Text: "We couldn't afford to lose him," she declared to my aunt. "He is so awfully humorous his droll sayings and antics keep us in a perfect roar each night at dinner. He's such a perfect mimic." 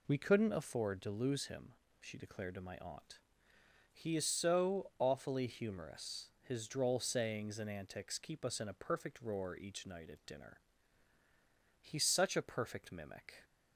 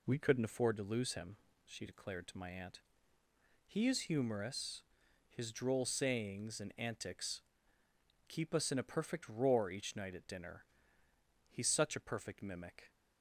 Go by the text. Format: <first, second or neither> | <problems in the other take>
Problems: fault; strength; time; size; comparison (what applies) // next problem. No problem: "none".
first | skips "so awfully"; at 4.0 s // pauses between "humorous" and "his"; noticeable; at 4.8 s; 0.46 s long // pauses between "antics" and "keep"; noticeable; at 7.4 s; 0.86 s long